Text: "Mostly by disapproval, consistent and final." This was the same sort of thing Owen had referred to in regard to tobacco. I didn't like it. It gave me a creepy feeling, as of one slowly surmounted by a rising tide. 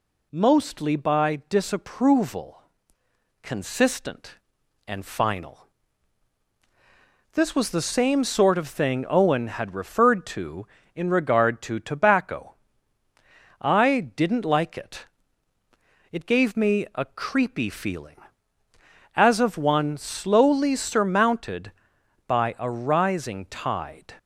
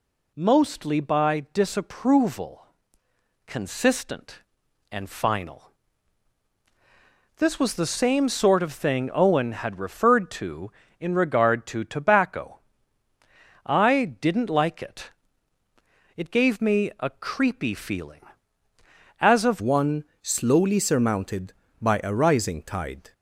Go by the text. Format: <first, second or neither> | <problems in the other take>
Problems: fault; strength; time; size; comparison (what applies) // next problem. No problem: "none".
first | changes voice at "one"; from 19.6 s on; 3.5 s long // pauses between "one" and "slowly"; slight; at 20.0 s; 0.16 s long